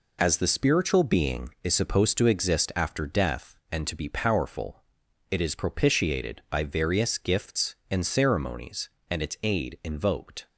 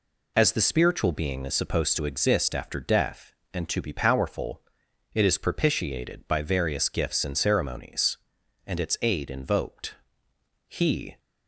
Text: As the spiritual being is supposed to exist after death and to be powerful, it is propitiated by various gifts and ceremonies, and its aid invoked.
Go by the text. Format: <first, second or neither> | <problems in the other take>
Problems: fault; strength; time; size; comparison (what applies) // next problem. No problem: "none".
first | goes on to say "He"; from 10.6 s on; 0.52 s long